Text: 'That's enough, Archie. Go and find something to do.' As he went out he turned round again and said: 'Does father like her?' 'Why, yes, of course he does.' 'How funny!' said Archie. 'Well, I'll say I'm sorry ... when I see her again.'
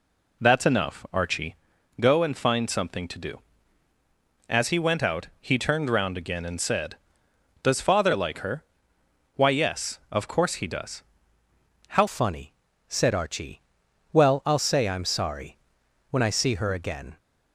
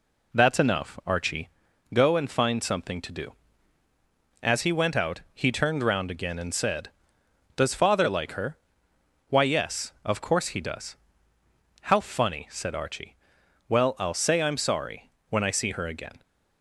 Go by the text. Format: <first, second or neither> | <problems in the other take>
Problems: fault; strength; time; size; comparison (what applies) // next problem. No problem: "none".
second | changes voice at "funny"; from 12.0 s on; 5.1 s long